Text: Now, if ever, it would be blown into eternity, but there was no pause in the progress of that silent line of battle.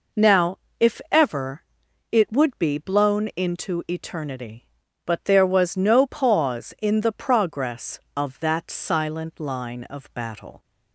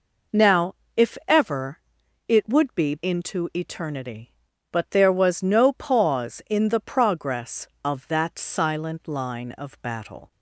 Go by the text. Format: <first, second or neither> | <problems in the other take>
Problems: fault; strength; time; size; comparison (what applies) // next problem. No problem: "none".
first | skips "blown"; at 2.9 s